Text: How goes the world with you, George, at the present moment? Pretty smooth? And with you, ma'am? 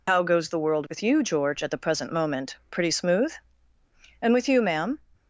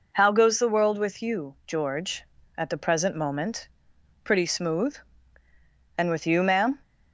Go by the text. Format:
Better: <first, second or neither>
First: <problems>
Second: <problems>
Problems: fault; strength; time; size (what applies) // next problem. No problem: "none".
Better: second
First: loses the start of "How"; at 0.0 s; 50 ms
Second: none